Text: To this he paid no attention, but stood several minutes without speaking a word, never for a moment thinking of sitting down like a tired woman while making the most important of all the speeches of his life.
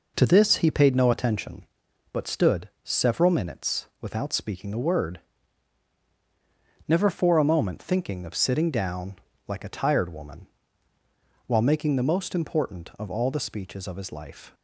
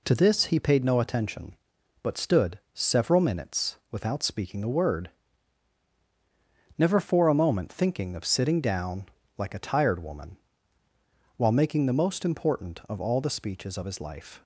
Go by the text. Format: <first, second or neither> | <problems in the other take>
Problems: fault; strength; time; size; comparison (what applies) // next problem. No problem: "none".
second | starts louder than the rest; noticeable; until 1.6 s; 5 dB // pauses between "stood" and "several"; slight; at 2.6 s; 0.16 s long; slight in the second // pauses between "down" and "like"; slight; at 9.1 s; 0.32 s long; slight in the second // pauses between "woman" and "while"; at 10.4 s; 1.0 s long; also in the second